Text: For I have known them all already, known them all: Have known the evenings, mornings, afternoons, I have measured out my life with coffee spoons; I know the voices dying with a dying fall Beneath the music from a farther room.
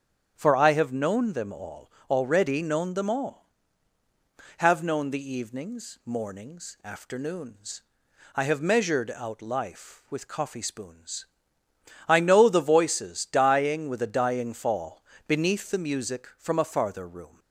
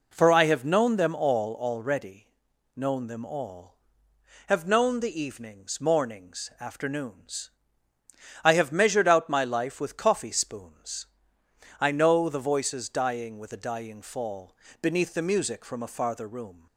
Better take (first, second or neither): second